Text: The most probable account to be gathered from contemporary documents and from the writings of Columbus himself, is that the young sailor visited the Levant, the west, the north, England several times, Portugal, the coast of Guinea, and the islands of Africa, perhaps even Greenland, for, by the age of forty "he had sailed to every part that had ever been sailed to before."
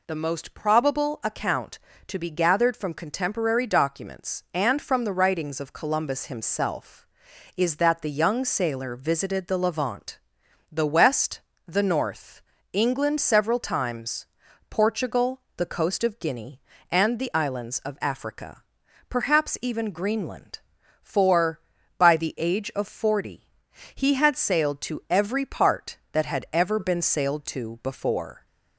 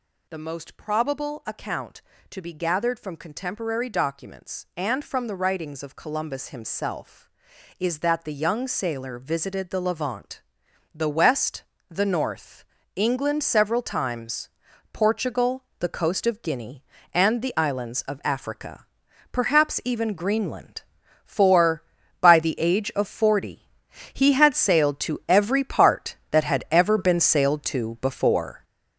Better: first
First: pauses between "forty" and "he"; noticeable; at 23.4 s; 0.46 s long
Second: gets louder; strong; throughout; 7.5 dB // pauses between "forty" and "he"; noticeable; at 23.6 s; 0.46 s long

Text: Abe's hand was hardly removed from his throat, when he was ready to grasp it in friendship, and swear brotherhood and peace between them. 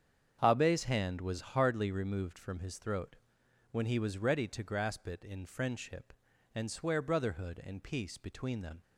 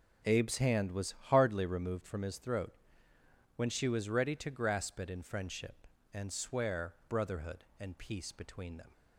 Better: first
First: starts louder than the rest; strong; until 1.4 s; 8 dB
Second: starts louder than the rest; strong; until 1.4 s; 9.5 dB // pauses between "was" and "hardly"; slight; at 1.1 s; 0.16 s long // says "she" for "he"; at 3.6 s

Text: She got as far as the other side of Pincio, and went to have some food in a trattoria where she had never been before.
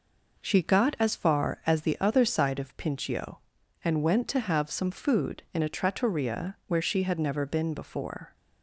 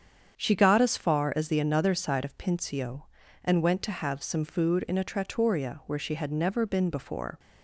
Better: first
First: none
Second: starts louder than the rest; strong; until 1.4 s; 7.5 dB // says "another" for "other"; at 1.6 s

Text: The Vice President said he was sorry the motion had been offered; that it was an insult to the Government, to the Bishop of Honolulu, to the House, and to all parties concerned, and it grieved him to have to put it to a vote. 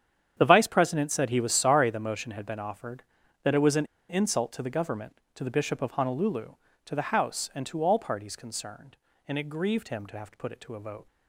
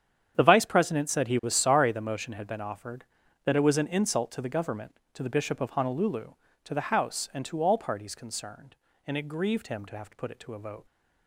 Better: second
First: starts louder than the rest; strong; until 1.3 s; 8.5 dB // pauses between "an" and "insult"; slight; at 3.8 s; 0.23 s long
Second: starts louder than the rest; strong; until 1.3 s; 8.5 dB

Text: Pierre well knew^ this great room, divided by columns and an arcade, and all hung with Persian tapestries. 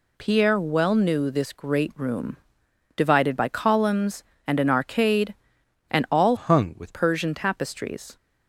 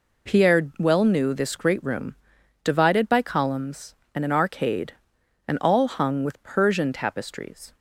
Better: second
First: changes voice from "hung" to "with"; from 6.3 to 6.9 s; 0.6 s long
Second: none

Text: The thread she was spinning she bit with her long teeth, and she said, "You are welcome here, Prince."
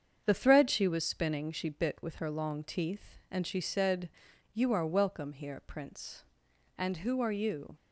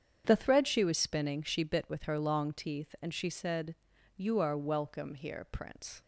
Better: second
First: starts louder than the rest; strong; until 1.2 s; 7.5 dB // goes on to say "And who are you"; noticeable; from 6.7 s on; 0.98 s long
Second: starts louder than the rest; strong; until 1.2 s; 8 dB

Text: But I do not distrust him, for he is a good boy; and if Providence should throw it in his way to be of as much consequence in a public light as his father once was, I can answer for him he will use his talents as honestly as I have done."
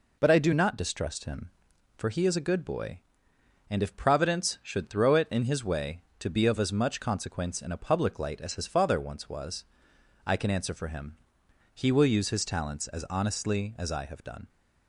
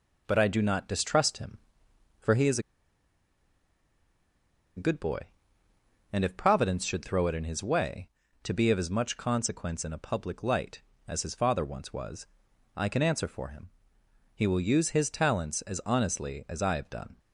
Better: first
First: pauses between "him" and "he"; noticeable; at 11.1 s; 0.58 s long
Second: pauses between "is" and "a"; strong; at 2.5 s; 2.1 s long // pauses between "him" and "he"; noticeable; at 13.6 s; 0.64 s long

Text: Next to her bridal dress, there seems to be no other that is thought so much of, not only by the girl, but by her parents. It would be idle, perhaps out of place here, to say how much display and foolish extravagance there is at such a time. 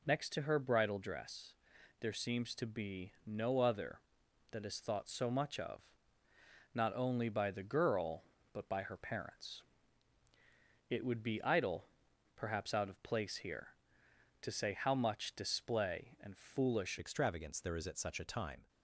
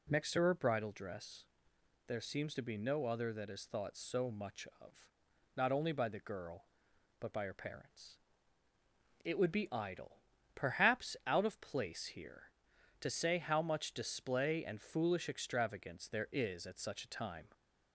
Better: second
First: changes voice at "extravagance"; from 16.9 s on; 1.7 s long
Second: none

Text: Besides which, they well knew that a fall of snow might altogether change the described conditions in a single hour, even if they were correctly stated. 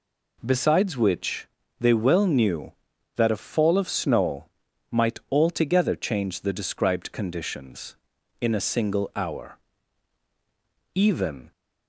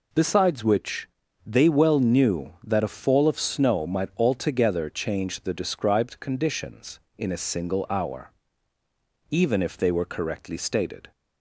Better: second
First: pauses between "snow" and "might"; at 4.4 s; 0.44 s long // stops before "if they were correctly stated"; at 11.5 s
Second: none

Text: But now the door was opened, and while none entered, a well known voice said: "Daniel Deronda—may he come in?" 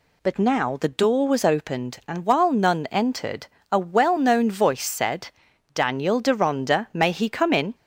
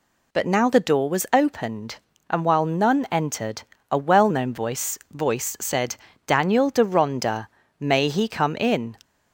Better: first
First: none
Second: says "voice" twice; at 5.1 s

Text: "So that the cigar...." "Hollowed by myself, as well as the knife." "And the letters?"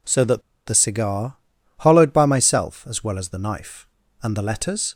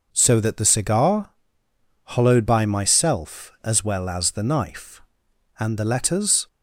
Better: second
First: pauses between "that" and "the"; slight; at 0.4 s; 0.25 s long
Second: none

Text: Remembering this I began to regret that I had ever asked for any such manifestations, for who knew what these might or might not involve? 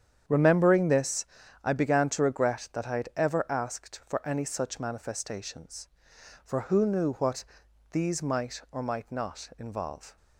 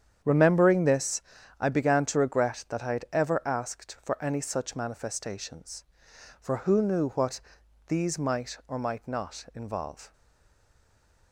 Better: first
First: starts louder than the rest; strong; until 1.6 s; 8.5 dB // pauses between "this" and "I"; slight; at 1.2 s; 0.36 s long // pauses between "what" and "these"; noticeable; at 7.4 s; 0.48 s long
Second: starts louder than the rest; strong; until 1.5 s; 8.5 dB // pauses between "this" and "I"; slight; at 1.2 s; 0.36 s long // pauses between "what" and "these"; noticeable; at 7.4 s; 0.48 s long // stays silent after the last word; noticeable; from 10.1 s on; 1.2 s long

